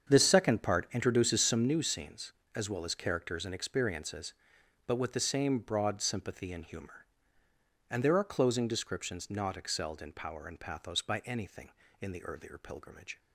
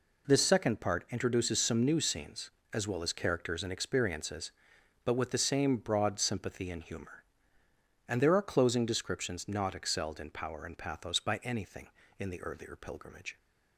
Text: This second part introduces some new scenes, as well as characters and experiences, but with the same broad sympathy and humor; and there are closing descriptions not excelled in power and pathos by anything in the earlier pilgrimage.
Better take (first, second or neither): second